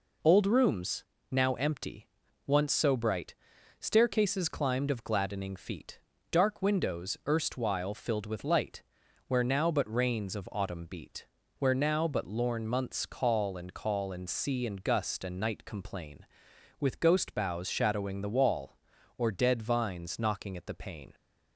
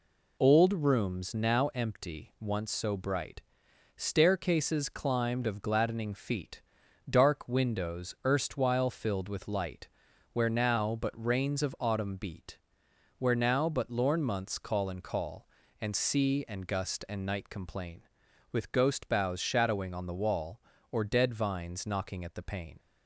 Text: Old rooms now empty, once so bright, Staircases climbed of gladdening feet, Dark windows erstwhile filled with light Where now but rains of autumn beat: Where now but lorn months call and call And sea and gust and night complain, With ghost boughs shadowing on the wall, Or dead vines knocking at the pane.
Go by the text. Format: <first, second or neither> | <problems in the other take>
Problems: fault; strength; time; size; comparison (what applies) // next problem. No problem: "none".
second | pauses between "rooms" and "now"; slight; at 1.0 s; 0.28 s long // pauses between "light" and "Where"; noticeable; at 8.8 s; 0.46 s long; noticeable in the second // skips "on"; at 18.2 s